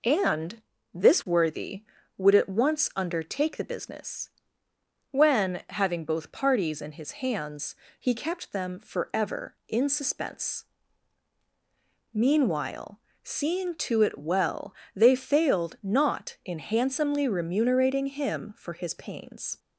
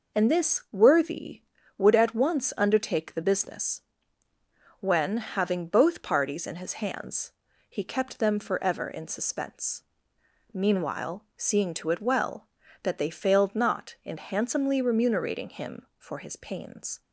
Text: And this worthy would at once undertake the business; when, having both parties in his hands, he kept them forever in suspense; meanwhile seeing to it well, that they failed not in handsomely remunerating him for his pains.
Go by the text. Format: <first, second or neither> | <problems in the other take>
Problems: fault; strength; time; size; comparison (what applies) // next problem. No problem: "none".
second | pauses between "And" and "this"; slight; at 0.6 s; 0.32 s long // pauses between "meanwhile" and "seeing"; slight; at 12.9 s; 0.24 s long // skips "that"; at 14.8 s